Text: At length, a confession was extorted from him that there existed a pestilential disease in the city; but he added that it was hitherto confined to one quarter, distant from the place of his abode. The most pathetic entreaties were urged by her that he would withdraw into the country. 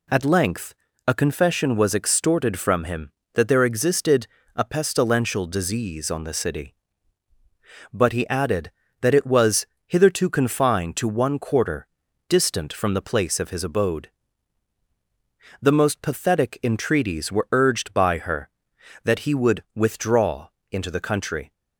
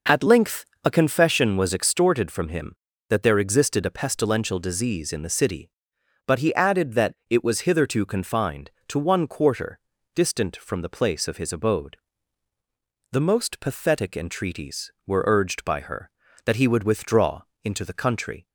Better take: second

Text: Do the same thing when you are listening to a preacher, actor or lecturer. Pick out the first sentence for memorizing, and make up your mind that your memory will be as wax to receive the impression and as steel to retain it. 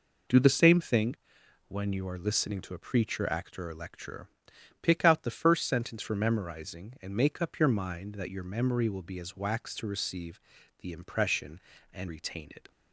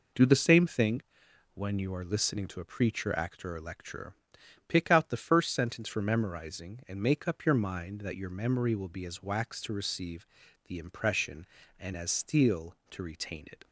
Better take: second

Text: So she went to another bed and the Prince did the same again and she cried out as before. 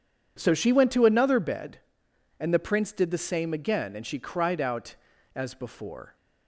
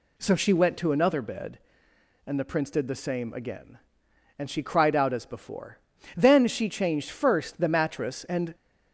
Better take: first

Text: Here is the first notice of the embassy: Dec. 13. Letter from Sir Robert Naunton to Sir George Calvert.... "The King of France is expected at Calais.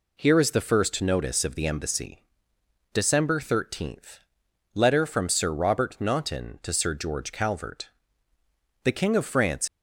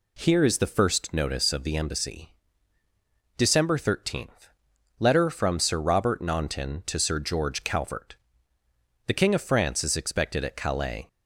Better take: second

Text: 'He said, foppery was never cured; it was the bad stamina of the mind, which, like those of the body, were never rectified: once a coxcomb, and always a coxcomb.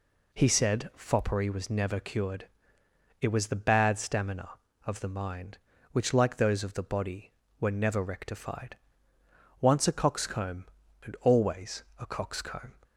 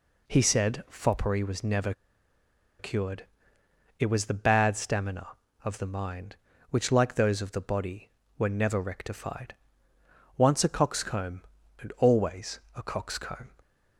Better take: first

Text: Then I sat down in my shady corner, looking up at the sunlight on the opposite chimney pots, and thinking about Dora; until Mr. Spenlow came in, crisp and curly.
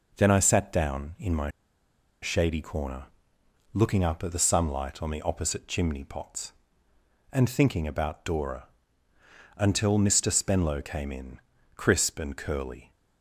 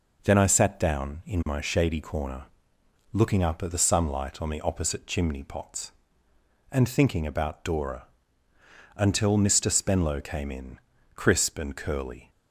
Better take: second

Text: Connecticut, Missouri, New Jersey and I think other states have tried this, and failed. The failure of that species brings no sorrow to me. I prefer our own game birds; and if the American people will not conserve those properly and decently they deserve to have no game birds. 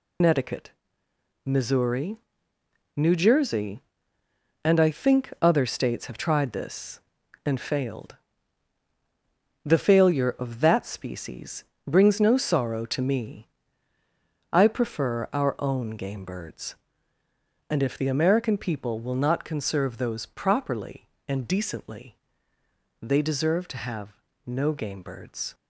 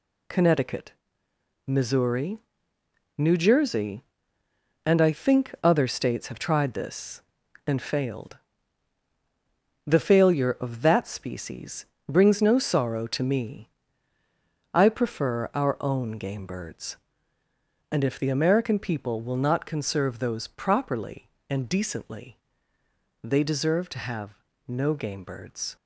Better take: second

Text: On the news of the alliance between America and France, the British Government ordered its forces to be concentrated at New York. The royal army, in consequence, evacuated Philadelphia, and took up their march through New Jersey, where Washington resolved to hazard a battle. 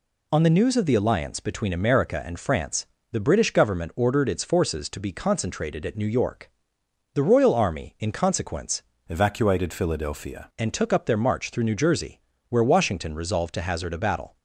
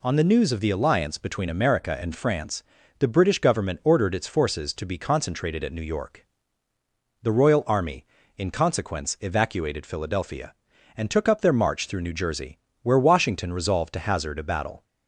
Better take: second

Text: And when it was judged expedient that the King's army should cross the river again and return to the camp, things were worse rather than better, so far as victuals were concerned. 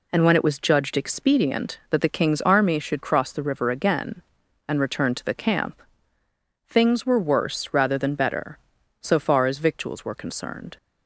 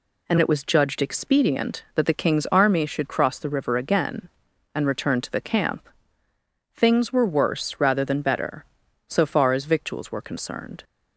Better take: first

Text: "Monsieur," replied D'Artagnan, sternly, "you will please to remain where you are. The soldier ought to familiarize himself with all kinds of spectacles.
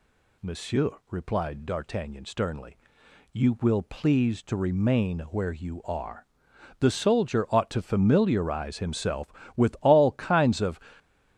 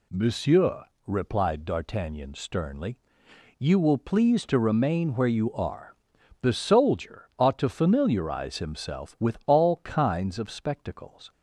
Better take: second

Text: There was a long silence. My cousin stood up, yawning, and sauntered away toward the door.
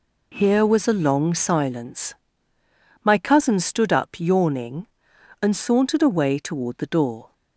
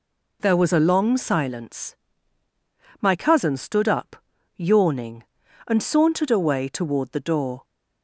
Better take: second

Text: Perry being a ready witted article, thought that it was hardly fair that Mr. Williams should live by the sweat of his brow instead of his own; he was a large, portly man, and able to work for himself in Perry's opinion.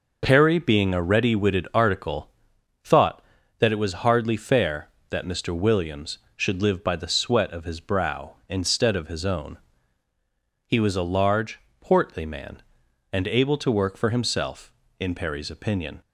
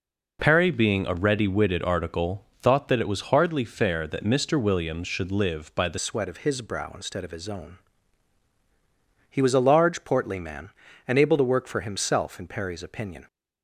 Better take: first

